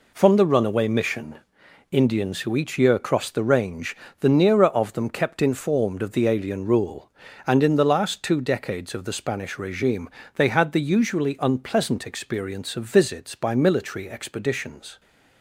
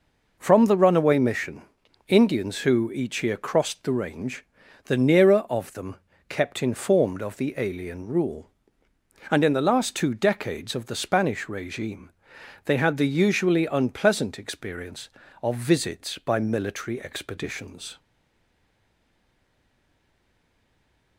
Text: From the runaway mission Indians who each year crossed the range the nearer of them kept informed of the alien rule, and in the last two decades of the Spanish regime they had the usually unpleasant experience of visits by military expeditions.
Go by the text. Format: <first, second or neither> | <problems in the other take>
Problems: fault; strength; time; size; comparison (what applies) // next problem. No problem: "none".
first | pauses between "mission" and "Indians"; at 1.6 s; 0.44 s long; noticeable in the first // pauses between "range" and "the"; at 4.4 s; 0.40 s long; slight in the first // pauses between "them" and "kept"; slight; at 5.9 s; 0.32 s long // pauses between "regime" and "they"; noticeable; at 12.1 s; 0.54 s long; slight in the first // stays silent after the last word; strong; from 17.9 s on; 3.2 s long